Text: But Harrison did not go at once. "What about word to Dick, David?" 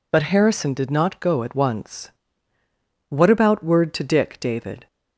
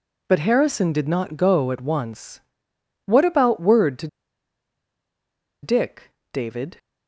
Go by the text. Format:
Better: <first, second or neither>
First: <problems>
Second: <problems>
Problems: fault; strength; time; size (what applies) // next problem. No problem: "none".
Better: first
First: none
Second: pauses between "to" and "Dick"; strong; at 4.0 s; 1.5 s long